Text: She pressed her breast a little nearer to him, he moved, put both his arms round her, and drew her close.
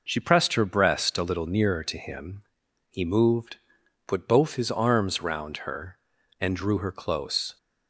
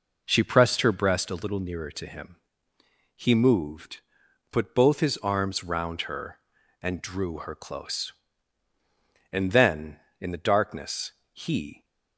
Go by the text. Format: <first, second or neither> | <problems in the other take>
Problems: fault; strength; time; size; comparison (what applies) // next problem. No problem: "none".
first | goes on to say "And then in the darkness he"; strong; from 9.3 s on; 2.5 s long